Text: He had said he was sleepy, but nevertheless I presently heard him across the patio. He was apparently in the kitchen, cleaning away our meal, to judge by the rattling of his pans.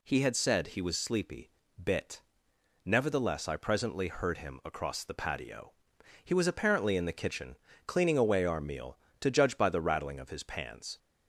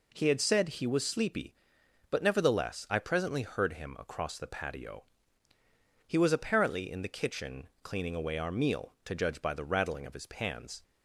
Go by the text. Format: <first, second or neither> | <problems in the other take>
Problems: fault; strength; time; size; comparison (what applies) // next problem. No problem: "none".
second | says "bit" for "but"; at 1.8 s